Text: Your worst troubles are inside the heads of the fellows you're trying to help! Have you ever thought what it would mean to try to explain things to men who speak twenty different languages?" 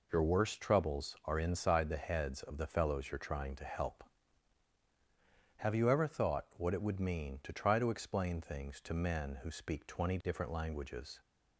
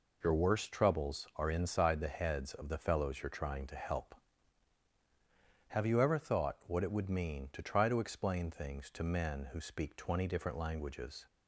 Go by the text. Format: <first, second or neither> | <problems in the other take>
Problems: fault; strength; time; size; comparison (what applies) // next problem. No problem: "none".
neither | none